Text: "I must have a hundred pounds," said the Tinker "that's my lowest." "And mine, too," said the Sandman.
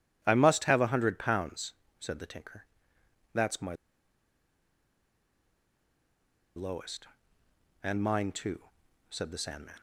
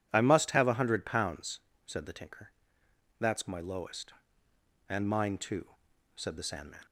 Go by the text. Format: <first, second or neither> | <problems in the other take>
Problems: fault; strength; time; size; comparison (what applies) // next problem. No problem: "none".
second | pauses between "Tinker" and "that's"; noticeable; at 2.6 s; 0.68 s long; noticeable in the second // pauses between "my" and "lowest"; strong; at 3.7 s; 2.8 s long